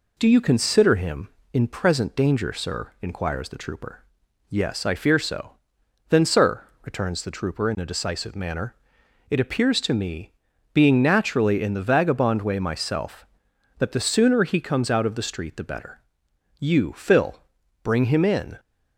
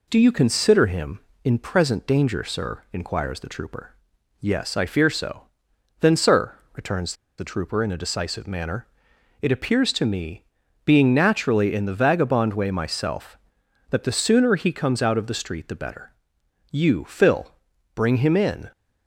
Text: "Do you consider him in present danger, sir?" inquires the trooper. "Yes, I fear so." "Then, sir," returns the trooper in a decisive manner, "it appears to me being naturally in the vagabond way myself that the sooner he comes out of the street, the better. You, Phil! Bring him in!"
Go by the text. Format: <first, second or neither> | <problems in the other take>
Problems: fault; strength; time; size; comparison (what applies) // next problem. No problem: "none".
first | pauses between "returns" and "the"; slight; at 7.1 s; 0.25 s long // pauses between "me" and "being"; at 10.4 s; 0.40 s long; also in the first